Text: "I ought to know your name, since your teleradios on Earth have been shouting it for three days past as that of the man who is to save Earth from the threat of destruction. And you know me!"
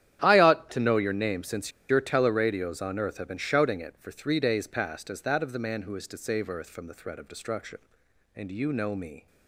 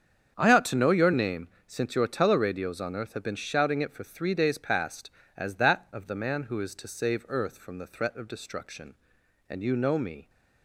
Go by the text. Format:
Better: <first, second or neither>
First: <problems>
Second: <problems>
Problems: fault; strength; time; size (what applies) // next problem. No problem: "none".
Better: second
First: starts louder than the rest; strong; until 1.2 s; 10.5 dB // pauses between "since" and "your"; slight; at 1.7 s; 0.19 s long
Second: starts louder than the rest; strong; until 1.3 s; 7.5 dB